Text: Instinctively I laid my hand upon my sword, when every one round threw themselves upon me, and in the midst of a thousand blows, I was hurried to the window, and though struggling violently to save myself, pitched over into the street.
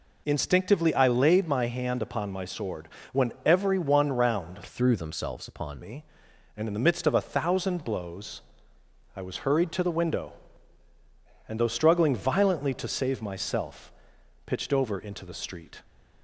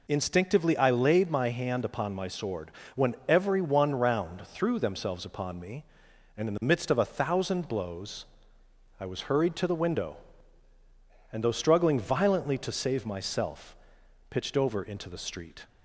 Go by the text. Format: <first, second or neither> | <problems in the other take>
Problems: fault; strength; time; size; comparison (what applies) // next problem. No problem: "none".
second | changes voice from "threw" to "upon"; from 4.6 to 5.8 s; 1.2 s long